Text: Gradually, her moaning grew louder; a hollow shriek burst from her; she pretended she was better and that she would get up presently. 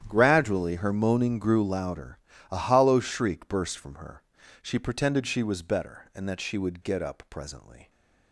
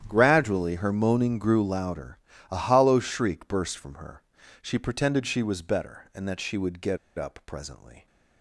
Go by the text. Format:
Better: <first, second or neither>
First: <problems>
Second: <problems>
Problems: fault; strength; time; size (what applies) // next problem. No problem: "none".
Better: first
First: starts louder than the rest; strong; until 1.0 s; 10 dB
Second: starts louder than the rest; strong; until 1.0 s; 10 dB // pauses between "get" and "up"; slight; at 6.9 s; 0.20 s long